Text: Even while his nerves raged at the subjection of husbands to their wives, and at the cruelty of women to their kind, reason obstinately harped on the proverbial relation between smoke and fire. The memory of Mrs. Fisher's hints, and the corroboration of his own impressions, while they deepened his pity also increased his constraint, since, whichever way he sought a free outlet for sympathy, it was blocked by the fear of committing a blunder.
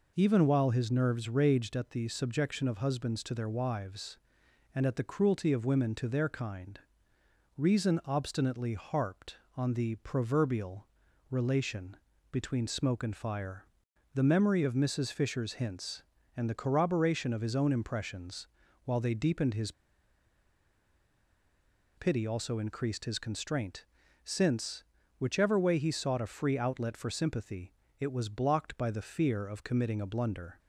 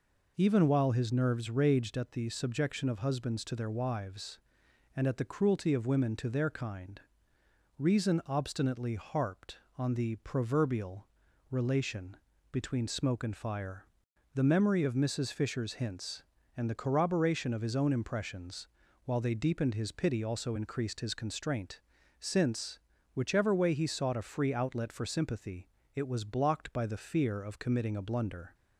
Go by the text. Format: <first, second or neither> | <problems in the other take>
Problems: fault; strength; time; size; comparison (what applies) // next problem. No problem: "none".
second | pauses between "proverbial" and "relation"; at 10.8 s; 0.44 s long; also in the second // pauses between "relation" and "between"; at 11.9 s; 0.38 s long; also in the second // pauses between "his" and "pity"; strong; at 19.7 s; 2.2 s long